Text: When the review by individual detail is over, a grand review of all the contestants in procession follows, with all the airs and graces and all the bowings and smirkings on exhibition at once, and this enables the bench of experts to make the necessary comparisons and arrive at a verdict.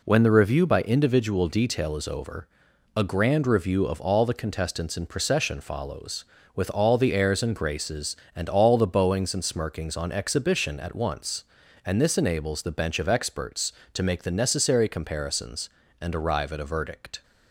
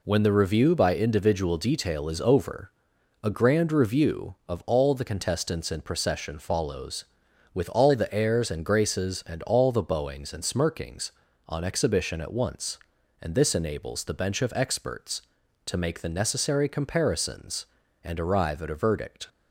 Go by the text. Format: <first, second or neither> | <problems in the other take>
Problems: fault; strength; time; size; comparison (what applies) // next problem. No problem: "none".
neither | none